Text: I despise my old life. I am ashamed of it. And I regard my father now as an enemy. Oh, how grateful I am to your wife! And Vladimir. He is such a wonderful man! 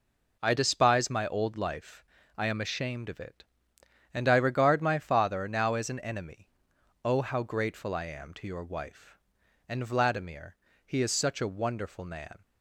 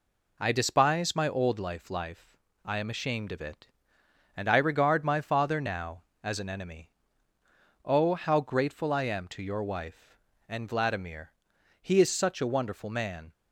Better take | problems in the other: first | says "life" twice; at 1.9 s

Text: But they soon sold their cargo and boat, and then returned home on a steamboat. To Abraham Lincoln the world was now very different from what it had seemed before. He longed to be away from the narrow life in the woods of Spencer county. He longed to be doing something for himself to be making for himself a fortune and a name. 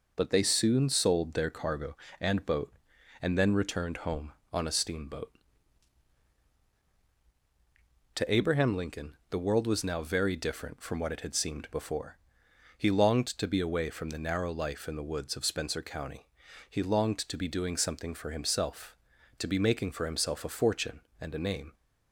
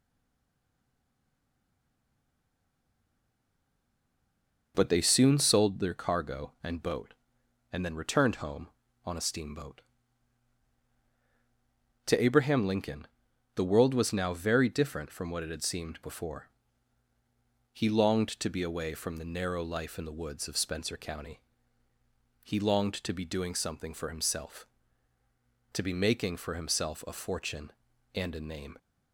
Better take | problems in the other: first | stays silent before the first word; strong; until 4.7 s; 4.7 s long // pauses between "Lincoln" and "the"; noticeable; at 13.0 s; 0.48 s long; slight in the first

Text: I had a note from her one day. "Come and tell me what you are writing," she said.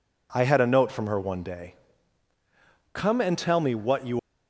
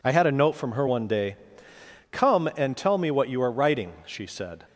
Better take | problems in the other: second | stops before "are writing she said"; at 4.1 s

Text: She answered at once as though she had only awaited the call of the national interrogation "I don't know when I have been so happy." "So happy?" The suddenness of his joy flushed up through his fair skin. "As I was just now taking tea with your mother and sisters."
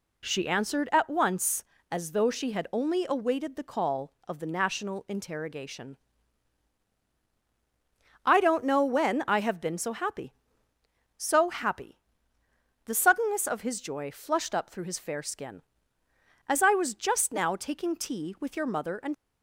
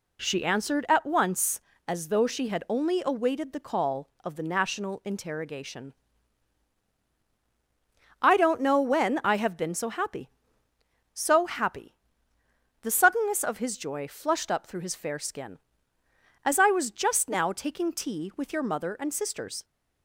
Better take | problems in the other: second | pauses between "interrogation" and "I"; strong; at 5.9 s; 2.2 s long; strong in the second // stops before "sisters"; at 19.1 s

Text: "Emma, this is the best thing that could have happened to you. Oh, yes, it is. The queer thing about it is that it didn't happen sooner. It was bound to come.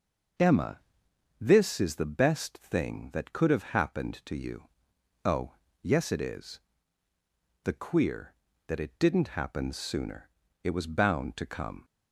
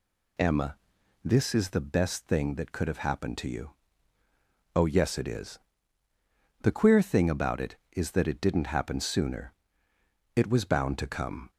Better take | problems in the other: second | skips "thing about it is"; at 8.4 s

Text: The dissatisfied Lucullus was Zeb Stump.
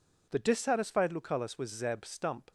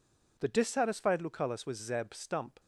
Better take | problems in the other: neither | none

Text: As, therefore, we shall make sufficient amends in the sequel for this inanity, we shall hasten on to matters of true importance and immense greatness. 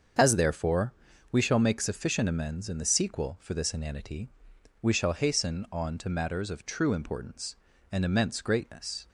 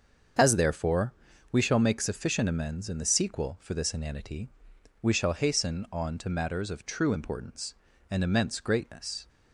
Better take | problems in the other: neither | starts louder than the rest; the same in both

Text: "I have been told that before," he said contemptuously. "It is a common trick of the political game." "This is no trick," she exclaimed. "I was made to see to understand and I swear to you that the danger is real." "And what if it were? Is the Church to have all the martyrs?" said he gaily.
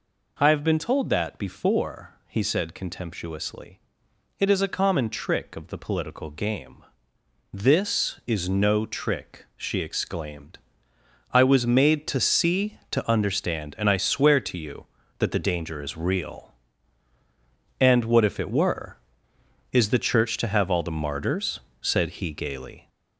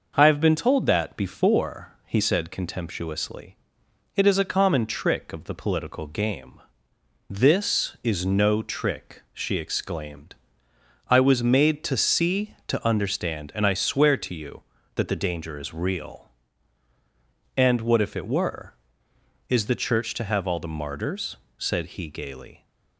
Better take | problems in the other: second | gets louder; noticeable; throughout; 4.5 dB

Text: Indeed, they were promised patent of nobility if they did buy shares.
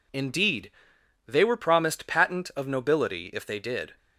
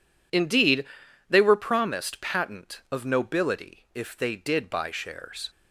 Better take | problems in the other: second | stops before "buy shares"; at 3.9 s

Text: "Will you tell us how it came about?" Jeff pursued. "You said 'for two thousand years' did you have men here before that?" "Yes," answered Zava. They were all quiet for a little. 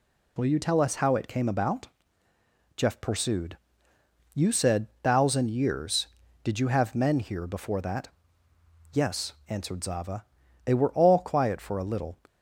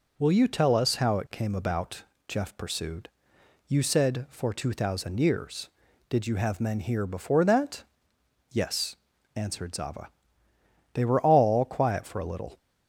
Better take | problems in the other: second | skips "for two"; at 4.9 s

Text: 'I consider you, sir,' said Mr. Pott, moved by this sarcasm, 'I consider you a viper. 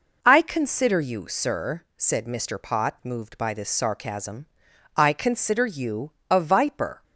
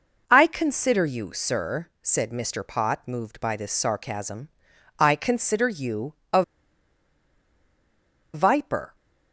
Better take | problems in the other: first | pauses between "you" and "a"; slight; at 6.1 s; 0.20 s long; slight in the first // pauses between "a" and "viper"; strong; at 6.4 s; 1.9 s long

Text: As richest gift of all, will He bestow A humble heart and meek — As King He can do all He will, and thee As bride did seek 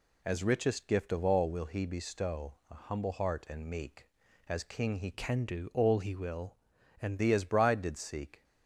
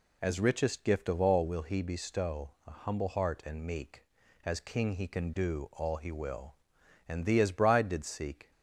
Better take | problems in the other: second | changes voice from "can" to "and"; from 5.1 to 7.1 s; 2.0 s long

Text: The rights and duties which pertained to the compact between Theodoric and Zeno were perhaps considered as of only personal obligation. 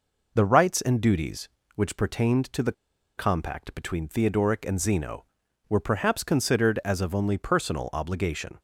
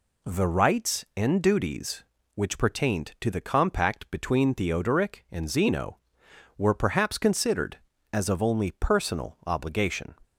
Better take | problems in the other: second | pauses between "the" and "compact"; at 2.7 s; 0.45 s long

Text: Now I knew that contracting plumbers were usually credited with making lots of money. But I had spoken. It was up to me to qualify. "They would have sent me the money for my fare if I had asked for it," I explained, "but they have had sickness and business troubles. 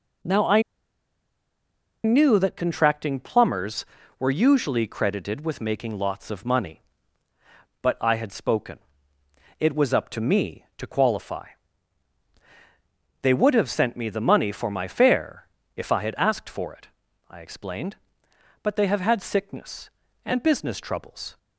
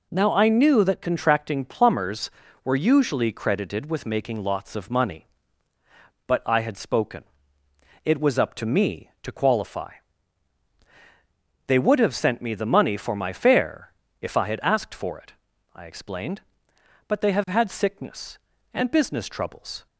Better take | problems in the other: second | pauses between "I" and "knew"; strong; at 0.6 s; 1.4 s long // pauses between "fare" and "if"; slight; at 15.4 s; 0.28 s long; slight in the second

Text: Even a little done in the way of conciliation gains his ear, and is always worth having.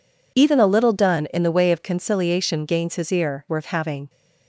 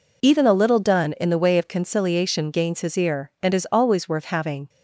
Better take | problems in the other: second | skips "and is always"; at 3.4 s

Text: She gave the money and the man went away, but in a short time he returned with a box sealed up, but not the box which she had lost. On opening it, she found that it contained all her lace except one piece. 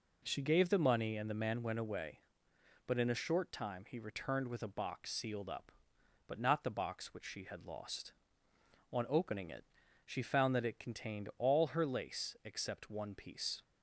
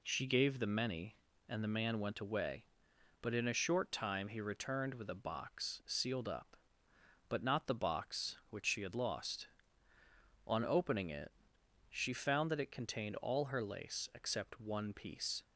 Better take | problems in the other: first | says "many" for "money"; at 0.6 s

